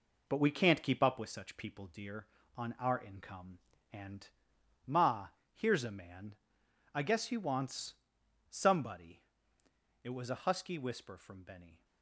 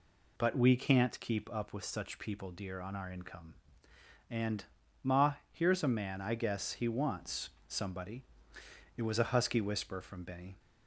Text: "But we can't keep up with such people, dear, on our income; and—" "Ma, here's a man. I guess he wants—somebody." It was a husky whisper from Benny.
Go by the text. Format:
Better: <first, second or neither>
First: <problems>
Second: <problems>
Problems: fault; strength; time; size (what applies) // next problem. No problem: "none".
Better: second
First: gets quieter; throughout; 6.5 dB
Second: none